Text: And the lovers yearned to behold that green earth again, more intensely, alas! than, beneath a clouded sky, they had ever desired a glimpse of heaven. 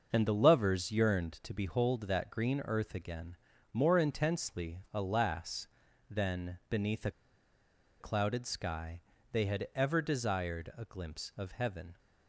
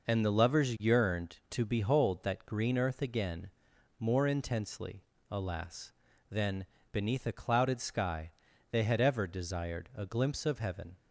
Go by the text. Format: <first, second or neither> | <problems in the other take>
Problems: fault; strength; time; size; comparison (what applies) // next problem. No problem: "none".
second | starts louder than the rest; until 1.1 s; 6 dB // pauses between "a" and "clouded"; noticeable; at 7.1 s; 0.90 s long